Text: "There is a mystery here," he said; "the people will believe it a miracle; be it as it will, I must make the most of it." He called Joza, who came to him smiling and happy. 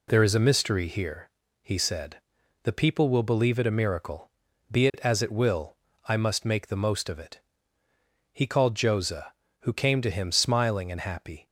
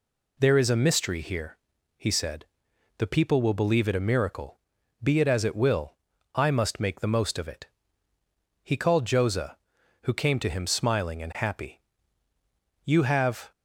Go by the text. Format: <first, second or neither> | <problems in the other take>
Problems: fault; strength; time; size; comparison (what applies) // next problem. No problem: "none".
first | goes on to say "You have"; noticeable; from 12.8 s on; 0.66 s long